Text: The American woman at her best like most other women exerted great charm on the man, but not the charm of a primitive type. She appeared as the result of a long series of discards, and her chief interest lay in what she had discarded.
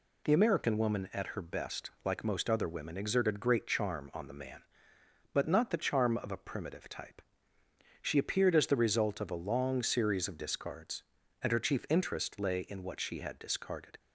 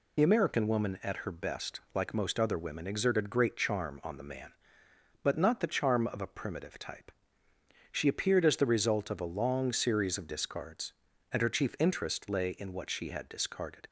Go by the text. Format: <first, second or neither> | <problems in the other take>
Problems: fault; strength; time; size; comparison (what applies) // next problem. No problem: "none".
first | loses the start of "The"; at 0.1 s; 30 ms